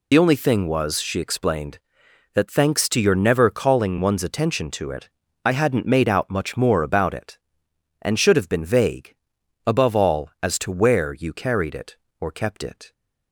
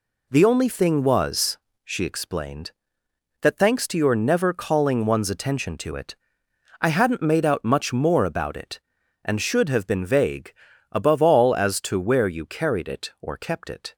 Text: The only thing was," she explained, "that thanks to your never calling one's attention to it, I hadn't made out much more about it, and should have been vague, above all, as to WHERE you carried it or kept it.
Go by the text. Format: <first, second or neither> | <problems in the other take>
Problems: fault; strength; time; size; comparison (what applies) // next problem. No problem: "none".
second | loses the start of "The"; at 0.1 s; 45 ms